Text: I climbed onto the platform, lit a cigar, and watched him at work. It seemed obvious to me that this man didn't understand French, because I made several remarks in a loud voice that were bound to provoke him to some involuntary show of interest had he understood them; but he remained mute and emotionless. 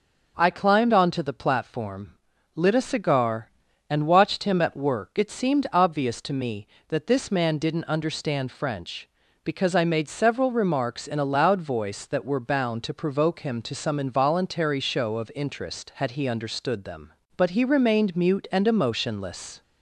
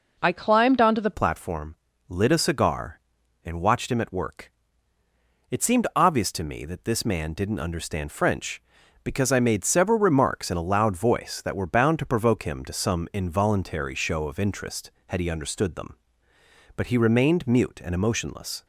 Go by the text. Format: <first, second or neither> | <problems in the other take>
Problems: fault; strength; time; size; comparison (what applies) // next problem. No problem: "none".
first | changes voice at "platform"; from 1.1 s on; 17.5 s long